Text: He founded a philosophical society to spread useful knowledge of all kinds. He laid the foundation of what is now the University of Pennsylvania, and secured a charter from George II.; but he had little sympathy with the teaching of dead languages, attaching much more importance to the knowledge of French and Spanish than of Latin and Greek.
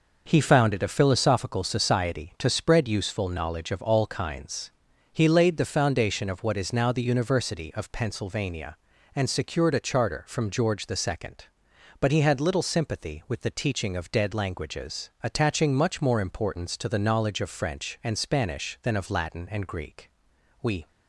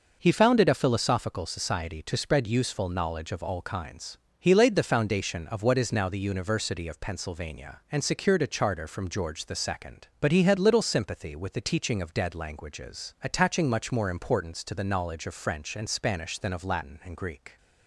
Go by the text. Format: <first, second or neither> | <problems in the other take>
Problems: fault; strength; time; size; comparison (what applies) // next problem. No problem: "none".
second | goes on to say "We"; slight; from 20.6 s on; 0.26 s long